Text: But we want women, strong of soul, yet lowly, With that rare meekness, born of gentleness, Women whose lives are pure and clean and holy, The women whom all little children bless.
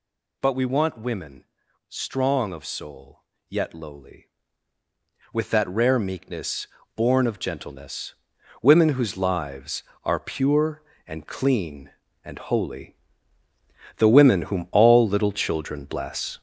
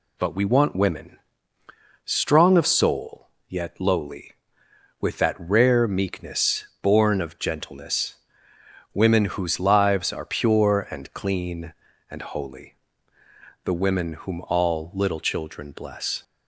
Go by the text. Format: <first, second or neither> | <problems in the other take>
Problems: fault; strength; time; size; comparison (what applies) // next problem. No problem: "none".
second | gets louder; throughout; 6.5 dB